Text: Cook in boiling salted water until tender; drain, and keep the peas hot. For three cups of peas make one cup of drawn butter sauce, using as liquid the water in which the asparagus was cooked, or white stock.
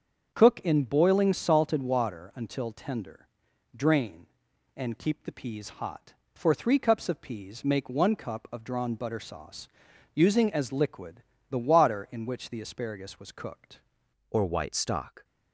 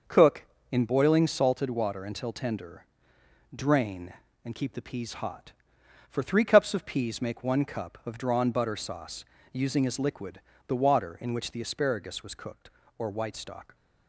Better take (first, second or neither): second